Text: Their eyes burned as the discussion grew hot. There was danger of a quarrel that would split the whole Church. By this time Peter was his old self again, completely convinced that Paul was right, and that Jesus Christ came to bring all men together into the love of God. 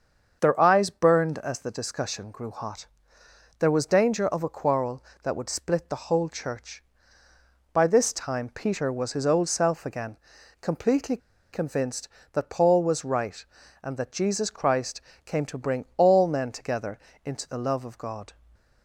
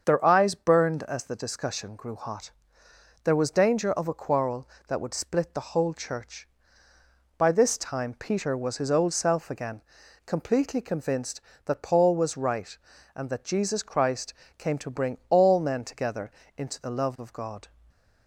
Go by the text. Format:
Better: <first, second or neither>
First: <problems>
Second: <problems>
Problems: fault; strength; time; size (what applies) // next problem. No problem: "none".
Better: second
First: starts louder than the rest; until 1.4 s; 6.5 dB // pauses between "completely" and "convinced"; slight; at 11.1 s; 0.35 s long // pauses between "Christ" and "came"; slight; at 15.0 s; 0.24 s long // pauses between "together" and "into"; slight; at 16.9 s; 0.28 s long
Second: starts louder than the rest; until 1.0 s; 6.5 dB // pauses between "Christ" and "came"; slight; at 14.3 s; 0.24 s long // pauses between "together" and "into"; slight; at 16.3 s; 0.28 s long